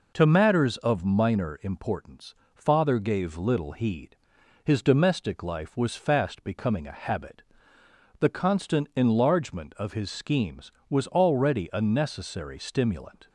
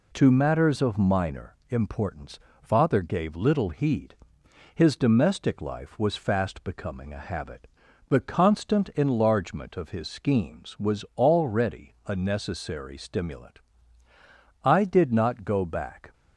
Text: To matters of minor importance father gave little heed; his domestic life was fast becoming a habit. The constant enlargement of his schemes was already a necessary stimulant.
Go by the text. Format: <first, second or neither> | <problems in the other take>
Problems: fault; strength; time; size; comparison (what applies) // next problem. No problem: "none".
first | pauses between "importance" and "father"; slight; at 2.3 s; 0.22 s long; slight in the first // goes on to say "I did not go back"; from 14.6 s on; 1.5 s long